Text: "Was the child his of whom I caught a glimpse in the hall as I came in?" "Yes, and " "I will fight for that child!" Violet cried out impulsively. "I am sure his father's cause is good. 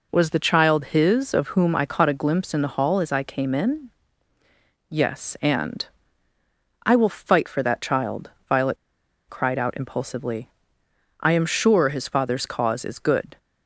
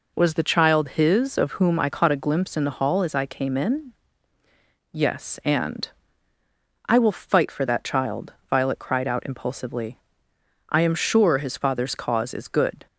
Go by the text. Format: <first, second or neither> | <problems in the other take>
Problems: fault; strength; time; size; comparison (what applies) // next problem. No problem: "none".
second | pauses between "Violet" and "cried"; noticeable; at 8.7 s; 0.52 s long